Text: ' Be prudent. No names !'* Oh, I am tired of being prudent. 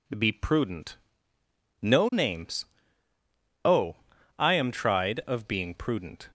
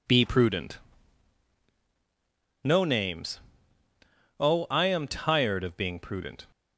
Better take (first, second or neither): second